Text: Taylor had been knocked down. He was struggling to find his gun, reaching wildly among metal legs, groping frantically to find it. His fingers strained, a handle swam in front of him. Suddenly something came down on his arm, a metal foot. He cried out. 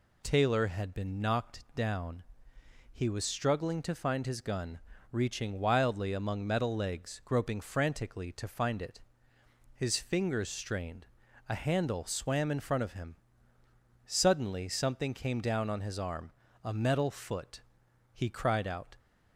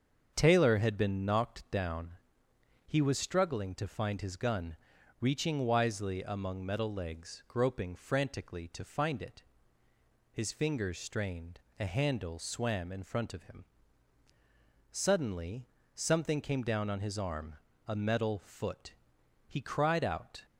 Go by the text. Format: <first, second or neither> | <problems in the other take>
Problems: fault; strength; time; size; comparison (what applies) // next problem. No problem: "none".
first | starts louder than the rest; until 1.3 s; 7 dB // says "wisely" for "wildly"; at 5.5 s // pauses between "Suddenly" and "something"; slight; at 15.6 s; 0.30 s long